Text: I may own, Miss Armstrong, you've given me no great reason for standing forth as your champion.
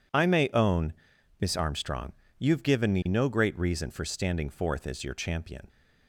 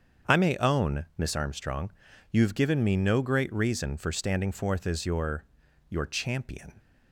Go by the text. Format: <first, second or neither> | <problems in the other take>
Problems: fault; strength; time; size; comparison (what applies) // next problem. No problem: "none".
first | starts louder than the rest; strong; until 1.3 s; 7 dB // says "your" twice; at 5.9 s